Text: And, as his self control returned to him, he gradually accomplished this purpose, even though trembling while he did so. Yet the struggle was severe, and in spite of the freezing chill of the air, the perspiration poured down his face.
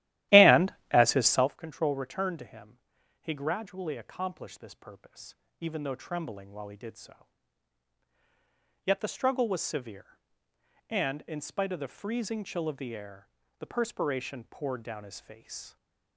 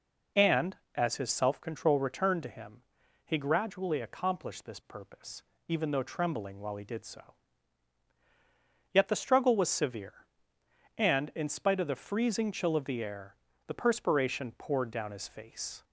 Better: second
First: starts louder than the rest; strong; until 1.5 s; 14.5 dB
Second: none

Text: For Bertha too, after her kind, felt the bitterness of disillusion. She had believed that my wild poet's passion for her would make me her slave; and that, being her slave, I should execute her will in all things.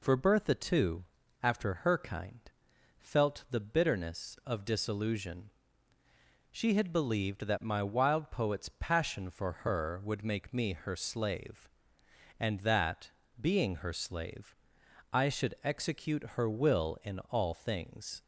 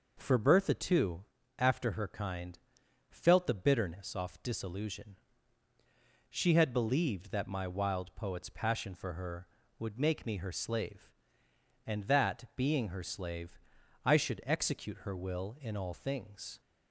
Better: first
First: none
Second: says "off" for "of"; at 4.1 s

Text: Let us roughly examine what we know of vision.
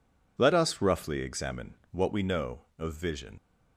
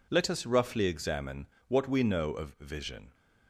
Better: second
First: pauses between "examine" and "what"; slight; at 1.7 s; 0.20 s long // leaves "vision" unfinished; at 3.3 s; 85 ms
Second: pauses between "examine" and "what"; slight; at 1.4 s; 0.22 s long

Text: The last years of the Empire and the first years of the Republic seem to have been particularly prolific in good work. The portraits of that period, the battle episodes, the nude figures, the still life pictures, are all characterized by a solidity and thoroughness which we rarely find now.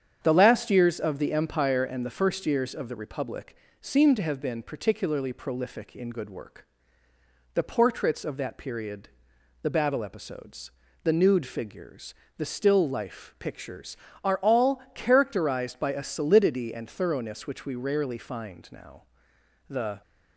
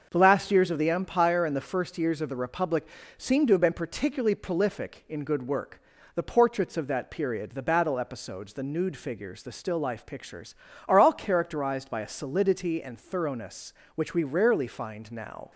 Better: second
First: starts louder than the rest; strong; until 1.2 s; 8 dB // pauses between "Republic" and "seem"; slight; at 3.5 s; 0.26 s long // goes on to say "The"; slight; from 19.7 s on; 0.30 s long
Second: starts louder than the rest; until 1.1 s; 6.5 dB // pauses between "Republic" and "seem"; slight; at 2.8 s; 0.30 s long

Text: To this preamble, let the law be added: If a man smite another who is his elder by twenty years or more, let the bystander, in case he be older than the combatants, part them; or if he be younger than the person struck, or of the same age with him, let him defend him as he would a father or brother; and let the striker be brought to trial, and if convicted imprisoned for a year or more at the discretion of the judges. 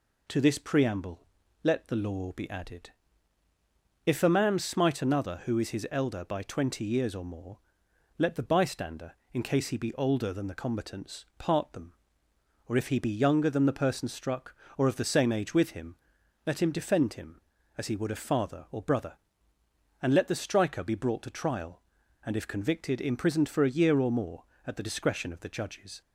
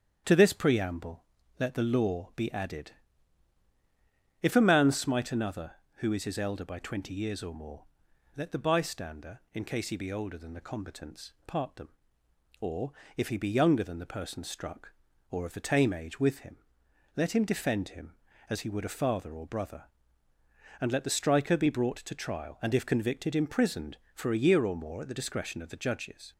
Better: first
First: none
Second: starts louder than the rest; strong; until 1.6 s; 8.5 dB // pauses between "or" and "if"; slight; at 12.9 s; 0.24 s long // says "tame" for "same"; at 15.6 s

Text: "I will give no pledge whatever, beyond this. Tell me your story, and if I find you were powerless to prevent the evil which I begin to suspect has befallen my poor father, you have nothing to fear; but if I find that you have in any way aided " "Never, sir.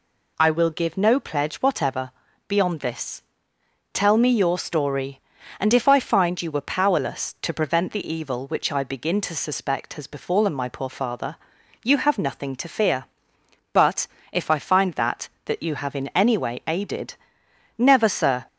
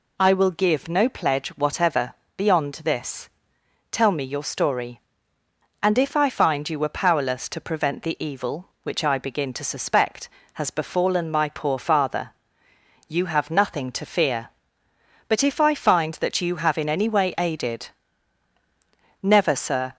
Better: second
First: pauses between "but" and "if"; slight; at 14.0 s; 0.24 s long // says "that" twice; at 15.4 s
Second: none

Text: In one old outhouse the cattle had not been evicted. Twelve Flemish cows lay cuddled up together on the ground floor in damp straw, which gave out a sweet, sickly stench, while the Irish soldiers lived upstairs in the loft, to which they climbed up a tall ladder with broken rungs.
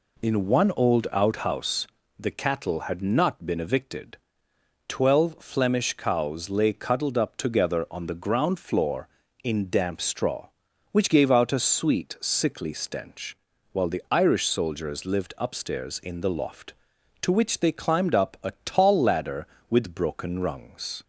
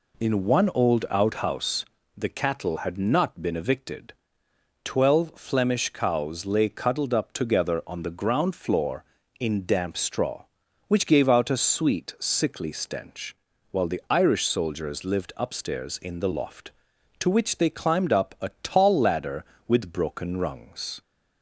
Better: neither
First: pauses between "outhouse" and "the"; slight; at 1.8 s; 0.32 s long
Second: pauses between "outhouse" and "the"; slight; at 1.8 s; 0.32 s long

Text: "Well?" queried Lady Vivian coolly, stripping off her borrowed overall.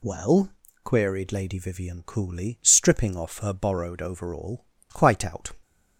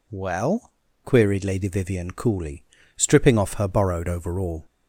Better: second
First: goes on to say "Quite out"; noticeable; from 4.8 s on; 0.64 s long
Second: none

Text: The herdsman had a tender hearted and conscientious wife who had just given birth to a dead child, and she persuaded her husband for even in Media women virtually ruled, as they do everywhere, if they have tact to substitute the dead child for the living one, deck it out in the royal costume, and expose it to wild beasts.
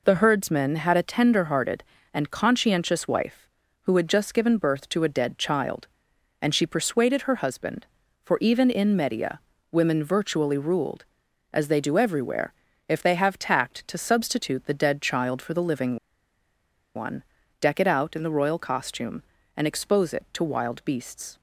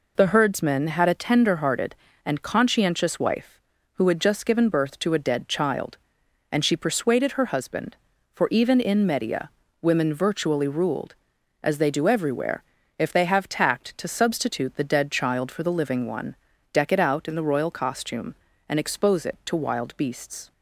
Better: second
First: pauses between "Media" and "women"; slight; at 9.4 s; 0.30 s long // pauses between "living" and "one"; at 15.9 s; 0.99 s long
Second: pauses between "Media" and "women"; slight; at 9.5 s; 0.30 s long

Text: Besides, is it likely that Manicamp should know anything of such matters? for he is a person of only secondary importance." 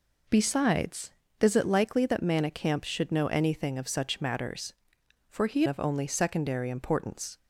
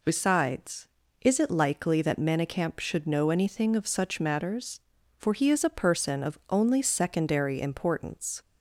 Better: second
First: skips "is a person"; at 5.6 s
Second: none

